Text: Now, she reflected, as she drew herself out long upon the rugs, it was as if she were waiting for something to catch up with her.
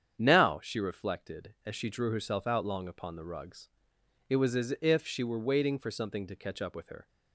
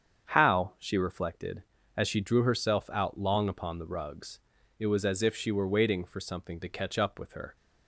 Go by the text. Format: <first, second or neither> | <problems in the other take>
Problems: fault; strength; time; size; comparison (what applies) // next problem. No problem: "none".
first | starts louder than the rest; strong; until 1.3 s; 7.5 dB; strong in the first // says "How" for "Now"; at 0.2 s